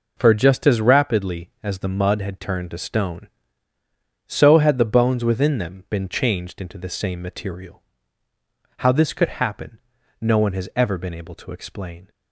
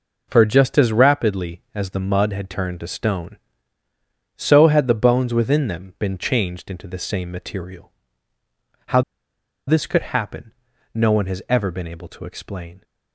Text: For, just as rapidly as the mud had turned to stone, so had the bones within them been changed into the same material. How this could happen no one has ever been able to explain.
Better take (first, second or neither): first